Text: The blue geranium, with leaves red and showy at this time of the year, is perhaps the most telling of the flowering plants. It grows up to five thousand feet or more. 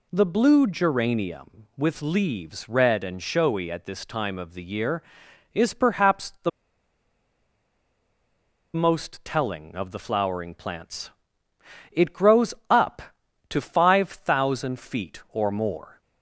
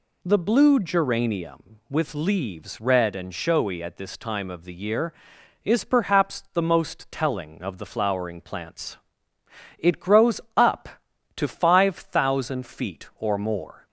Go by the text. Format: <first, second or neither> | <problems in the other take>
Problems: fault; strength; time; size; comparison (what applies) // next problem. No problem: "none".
second | pauses between "the" and "most"; strong; at 6.4 s; 2.2 s long // pauses between "grows" and "up"; slight; at 12.5 s; 0.16 s long; slight in the second